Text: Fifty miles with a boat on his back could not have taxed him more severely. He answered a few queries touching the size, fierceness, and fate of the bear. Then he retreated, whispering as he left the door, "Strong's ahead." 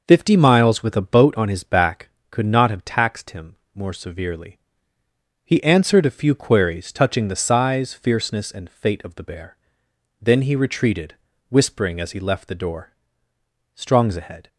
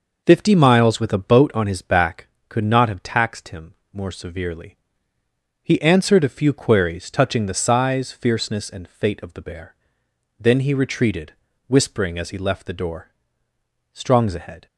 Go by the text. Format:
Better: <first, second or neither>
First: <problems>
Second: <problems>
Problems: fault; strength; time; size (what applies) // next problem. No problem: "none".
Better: neither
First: pauses between "him" and "more"; slight; at 3.5 s; 0.18 s long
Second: pauses between "him" and "more"; slight; at 3.7 s; 0.18 s long